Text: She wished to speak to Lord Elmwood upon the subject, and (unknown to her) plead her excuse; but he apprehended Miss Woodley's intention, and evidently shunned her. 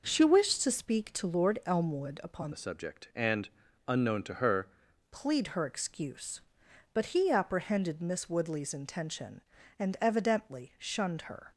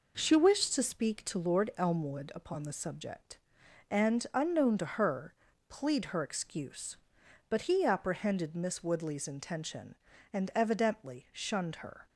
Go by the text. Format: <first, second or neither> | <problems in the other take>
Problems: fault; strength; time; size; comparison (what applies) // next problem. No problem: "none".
second | changes voice from "the" to "her"; from 2.5 to 4.6 s; 2.1 s long